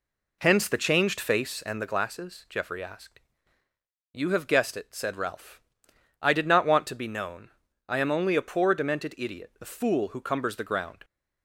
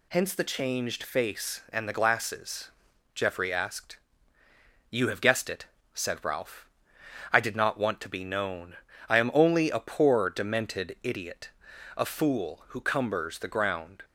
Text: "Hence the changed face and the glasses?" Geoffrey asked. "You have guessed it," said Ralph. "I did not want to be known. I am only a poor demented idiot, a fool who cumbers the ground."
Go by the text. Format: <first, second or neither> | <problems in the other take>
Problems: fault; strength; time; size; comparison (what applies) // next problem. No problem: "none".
second | starts louder than the rest; slight; until 1.9 s; 3 dB